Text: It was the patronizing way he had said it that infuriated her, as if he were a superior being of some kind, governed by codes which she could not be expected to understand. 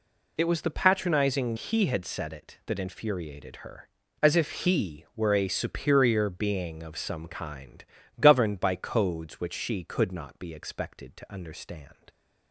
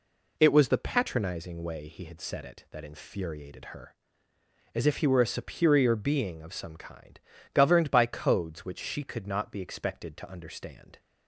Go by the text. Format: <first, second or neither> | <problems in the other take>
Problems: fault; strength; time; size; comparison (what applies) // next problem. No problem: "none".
second | skips "way"; at 1.5 s